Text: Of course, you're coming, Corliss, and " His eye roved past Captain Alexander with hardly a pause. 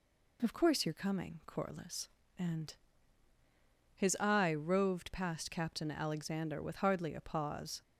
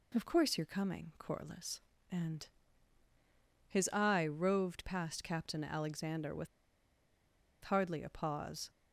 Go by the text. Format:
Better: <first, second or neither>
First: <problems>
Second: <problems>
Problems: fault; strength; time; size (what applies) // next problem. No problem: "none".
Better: first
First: none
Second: pauses between "with" and "hardly"; at 6.4 s; 1.1 s long